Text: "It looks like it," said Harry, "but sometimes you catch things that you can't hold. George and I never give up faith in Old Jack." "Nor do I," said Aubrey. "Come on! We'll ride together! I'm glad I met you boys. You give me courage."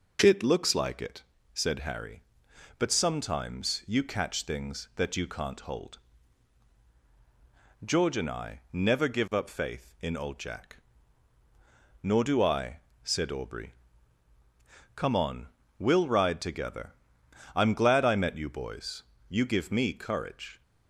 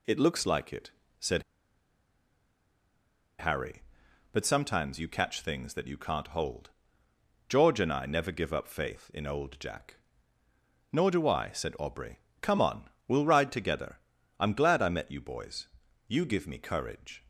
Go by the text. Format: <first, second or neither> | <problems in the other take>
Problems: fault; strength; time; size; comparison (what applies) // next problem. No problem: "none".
first | pauses between "said" and "Harry"; strong; at 1.4 s; 1.9 s long